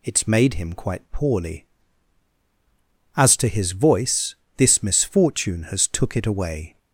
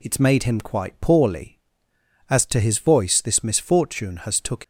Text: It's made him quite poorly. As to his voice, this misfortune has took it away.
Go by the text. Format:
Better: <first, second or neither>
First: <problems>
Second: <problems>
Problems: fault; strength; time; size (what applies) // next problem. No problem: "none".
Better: first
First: none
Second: stops before "it away"; at 4.6 s